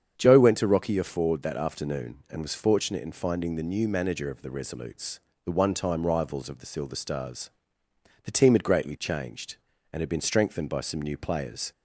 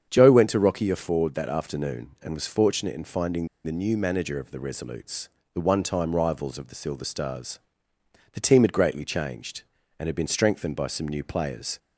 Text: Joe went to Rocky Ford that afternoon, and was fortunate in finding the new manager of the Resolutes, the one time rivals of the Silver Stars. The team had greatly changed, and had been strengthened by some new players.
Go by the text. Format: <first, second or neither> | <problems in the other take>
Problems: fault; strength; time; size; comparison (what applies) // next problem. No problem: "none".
first | starts louder than the rest; strong; until 1.1 s; 7.5 dB; strong in the first // pauses between "finding" and "the"; slight; at 3.4 s; 0.17 s long